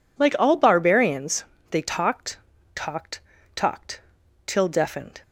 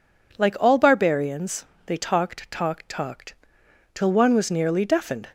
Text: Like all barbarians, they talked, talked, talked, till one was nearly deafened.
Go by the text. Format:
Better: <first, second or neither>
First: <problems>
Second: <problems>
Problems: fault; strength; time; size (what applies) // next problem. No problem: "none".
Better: second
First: skips "one was nearly"; at 4.6 s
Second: none